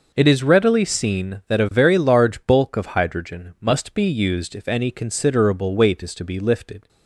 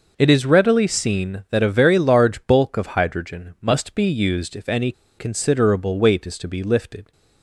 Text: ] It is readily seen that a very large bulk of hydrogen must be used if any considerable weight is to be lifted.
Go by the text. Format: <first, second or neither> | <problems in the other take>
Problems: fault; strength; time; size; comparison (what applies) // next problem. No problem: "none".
first | pauses between "any" and "considerable"; slight; at 4.9 s; 0.25 s long